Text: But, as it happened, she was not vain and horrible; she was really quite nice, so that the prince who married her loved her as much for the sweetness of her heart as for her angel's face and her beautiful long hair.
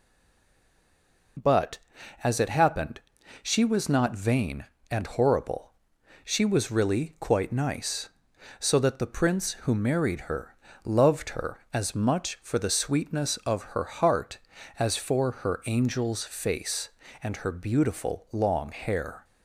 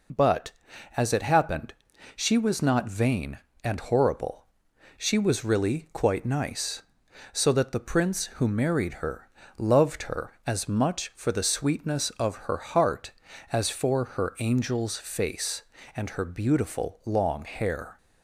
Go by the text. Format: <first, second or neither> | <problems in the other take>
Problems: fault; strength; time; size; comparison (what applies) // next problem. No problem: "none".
second | stays silent before the first word; noticeable; until 1.3 s; 1.3 s long // pauses between "her" and "loved"; slight; at 10.5 s; 0.28 s long; slight in the second